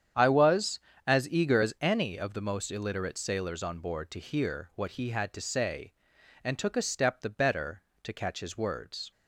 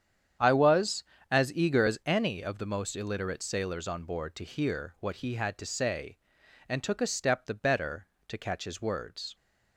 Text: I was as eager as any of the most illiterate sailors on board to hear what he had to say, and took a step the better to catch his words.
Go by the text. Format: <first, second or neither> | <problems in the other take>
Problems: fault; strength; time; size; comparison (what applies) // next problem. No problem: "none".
neither | starts louder than the rest; strong; the same in both